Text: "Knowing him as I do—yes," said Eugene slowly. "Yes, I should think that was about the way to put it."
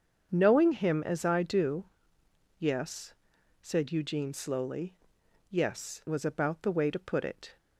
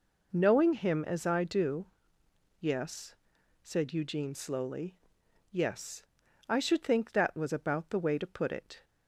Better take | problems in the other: second | starts louder than the rest; until 1.3 s; 7 dB // skips "I should think that"; at 6.0 s

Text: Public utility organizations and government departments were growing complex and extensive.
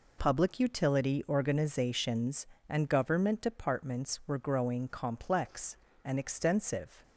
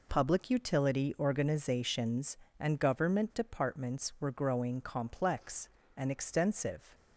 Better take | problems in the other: neither | none

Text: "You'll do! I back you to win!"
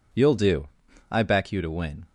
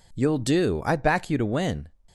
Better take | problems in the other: neither | none

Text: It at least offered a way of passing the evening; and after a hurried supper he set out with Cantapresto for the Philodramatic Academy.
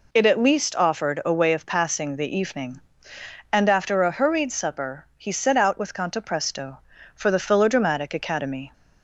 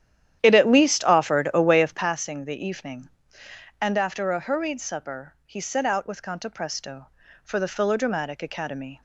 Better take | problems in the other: first | starts louder than the rest; strong; until 2.2 s; 10.5 dB

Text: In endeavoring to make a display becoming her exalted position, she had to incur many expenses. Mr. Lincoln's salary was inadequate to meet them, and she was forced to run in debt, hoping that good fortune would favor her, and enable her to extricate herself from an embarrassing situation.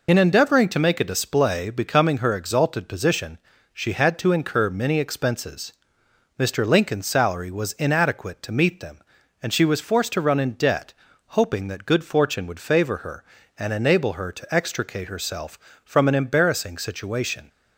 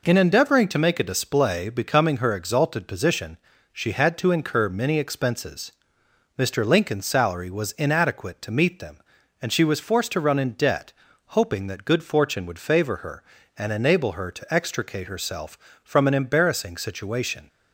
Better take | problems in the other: second | loses the start of "In"; at 0.0 s; 45 ms

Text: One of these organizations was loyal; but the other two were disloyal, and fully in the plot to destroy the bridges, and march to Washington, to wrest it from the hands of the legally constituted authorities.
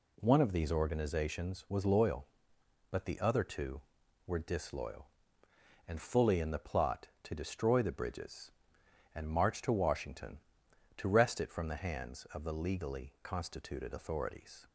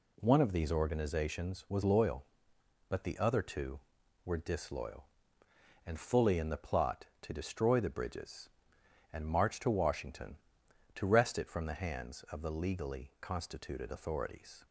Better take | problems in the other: neither | none

